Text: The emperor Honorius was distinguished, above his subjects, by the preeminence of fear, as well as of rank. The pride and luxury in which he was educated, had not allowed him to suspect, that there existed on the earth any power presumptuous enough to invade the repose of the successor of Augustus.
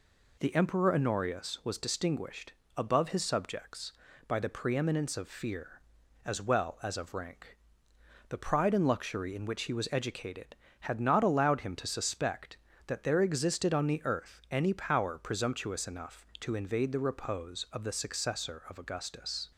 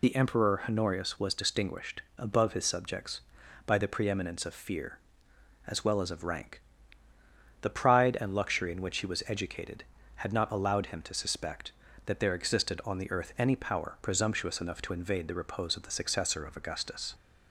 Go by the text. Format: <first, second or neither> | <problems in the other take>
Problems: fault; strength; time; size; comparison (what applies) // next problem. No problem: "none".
first | loses the start of "The"; at 0.0 s; 25 ms